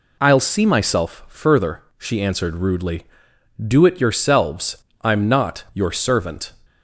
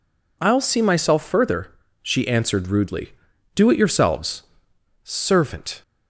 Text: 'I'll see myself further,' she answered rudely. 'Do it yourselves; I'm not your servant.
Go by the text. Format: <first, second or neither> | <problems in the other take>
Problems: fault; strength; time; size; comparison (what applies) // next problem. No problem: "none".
first | skips "I'm not your"; at 4.7 s